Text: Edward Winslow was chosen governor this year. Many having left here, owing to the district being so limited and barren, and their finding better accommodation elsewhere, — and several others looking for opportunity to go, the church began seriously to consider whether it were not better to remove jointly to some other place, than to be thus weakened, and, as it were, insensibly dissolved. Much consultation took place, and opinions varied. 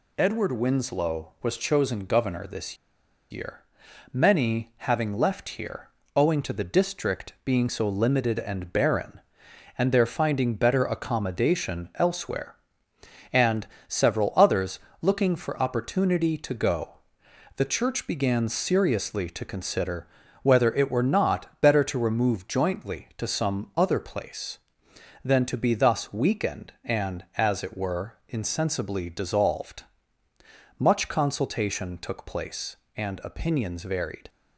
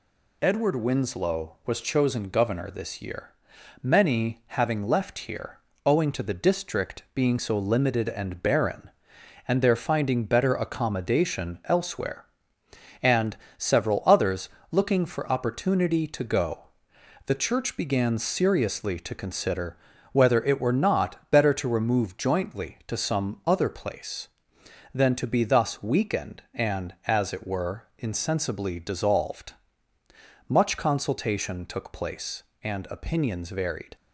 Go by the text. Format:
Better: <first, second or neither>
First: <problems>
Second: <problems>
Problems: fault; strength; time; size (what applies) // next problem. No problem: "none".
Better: second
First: pauses between "this" and "year"; noticeable; at 2.7 s; 0.54 s long // pauses between "and" and "several"; slight; at 13.6 s; 0.20 s long // pauses between "others" and "looking"; slight; at 14.7 s; 0.22 s long // pauses between "consider" and "whether"; slight; at 20.0 s; 0.36 s long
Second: pauses between "and" and "several"; slight; at 13.3 s; 0.20 s long // pauses between "others" and "looking"; slight; at 14.4 s; 0.22 s long // pauses between "consider" and "whether"; slight; at 19.7 s; 0.36 s long